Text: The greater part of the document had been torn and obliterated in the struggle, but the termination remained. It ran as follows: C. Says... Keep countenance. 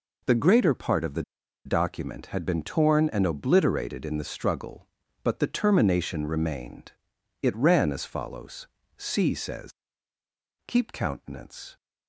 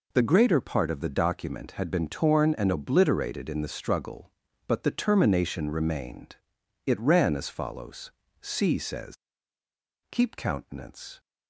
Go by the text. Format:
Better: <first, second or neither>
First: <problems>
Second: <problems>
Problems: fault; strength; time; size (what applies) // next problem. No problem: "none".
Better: second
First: pauses between "the" and "document"; at 1.2 s; 0.42 s long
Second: none